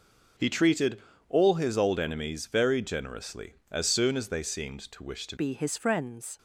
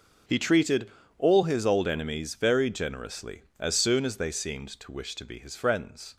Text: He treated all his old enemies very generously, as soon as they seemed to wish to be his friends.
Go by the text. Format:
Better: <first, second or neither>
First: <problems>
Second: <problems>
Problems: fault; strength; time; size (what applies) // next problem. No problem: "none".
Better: second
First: pauses between "treated" and "all"; slight; at 1.0 s; 0.28 s long // changes voice at "be"; from 5.3 s on; 1.0 s long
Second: pauses between "treated" and "all"; slight; at 0.9 s; 0.28 s long